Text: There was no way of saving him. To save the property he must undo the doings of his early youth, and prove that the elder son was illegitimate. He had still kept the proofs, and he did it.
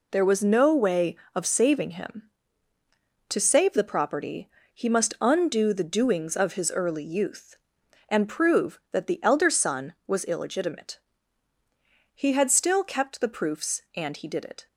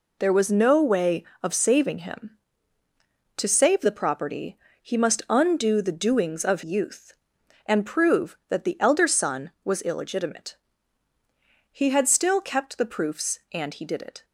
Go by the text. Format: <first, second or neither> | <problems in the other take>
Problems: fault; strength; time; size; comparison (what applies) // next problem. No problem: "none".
first | pauses between "property" and "he"; slight; at 4.5 s; 0.24 s long; slight in the first // skips "his early"; at 6.6 s